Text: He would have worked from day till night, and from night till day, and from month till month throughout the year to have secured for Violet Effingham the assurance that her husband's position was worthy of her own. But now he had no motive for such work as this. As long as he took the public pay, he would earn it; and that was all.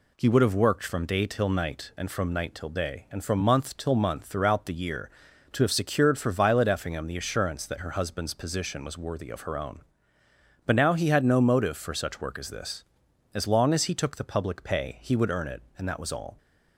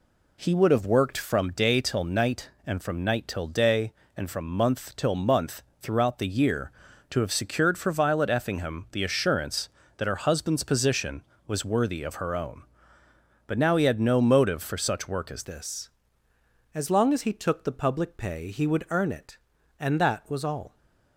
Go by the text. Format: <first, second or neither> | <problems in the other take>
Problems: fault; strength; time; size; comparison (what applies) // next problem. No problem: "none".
first | pauses between "month" and "throughout"; slight; at 5.6 s; 0.20 s long // changes voice at "this"; from 15.4 s on; 5.3 s long